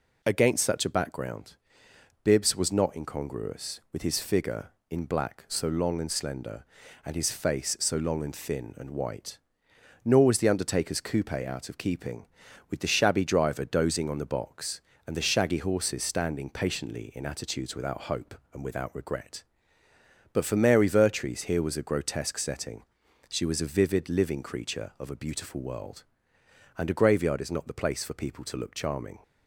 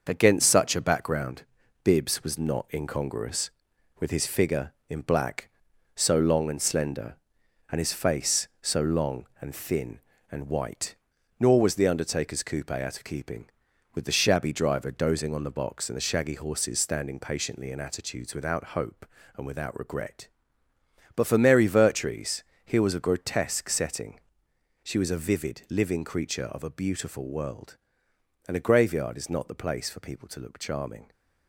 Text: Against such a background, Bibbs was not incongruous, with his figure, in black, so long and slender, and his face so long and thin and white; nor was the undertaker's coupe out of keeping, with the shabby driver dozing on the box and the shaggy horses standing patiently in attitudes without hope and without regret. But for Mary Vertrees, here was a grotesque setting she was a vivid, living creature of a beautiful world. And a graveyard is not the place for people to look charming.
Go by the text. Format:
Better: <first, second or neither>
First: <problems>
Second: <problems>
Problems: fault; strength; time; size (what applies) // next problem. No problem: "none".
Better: first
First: pauses between "setting" and "she"; at 22.8 s; 0.44 s long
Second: gets quieter; noticeable; throughout; 6 dB // pauses between "setting" and "she"; noticeable; at 24.1 s; 0.64 s long